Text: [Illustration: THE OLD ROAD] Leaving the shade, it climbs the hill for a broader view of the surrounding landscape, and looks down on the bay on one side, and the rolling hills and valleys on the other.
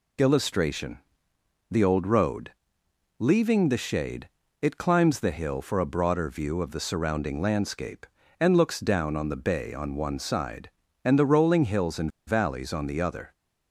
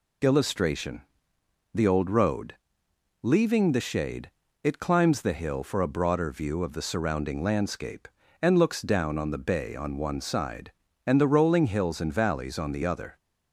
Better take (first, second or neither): second